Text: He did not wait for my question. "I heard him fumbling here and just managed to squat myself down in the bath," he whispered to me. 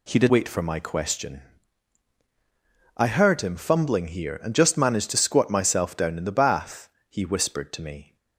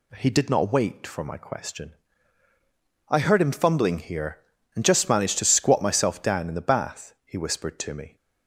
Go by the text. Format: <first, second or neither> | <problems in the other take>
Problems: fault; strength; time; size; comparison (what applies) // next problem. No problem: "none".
second | skips "not"; at 0.2 s